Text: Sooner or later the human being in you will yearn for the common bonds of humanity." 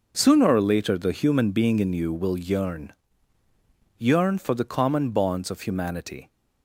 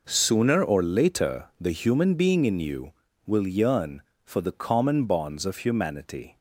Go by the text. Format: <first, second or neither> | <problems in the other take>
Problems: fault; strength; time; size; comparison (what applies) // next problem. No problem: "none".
second | says "yearn" twice; at 3.9 s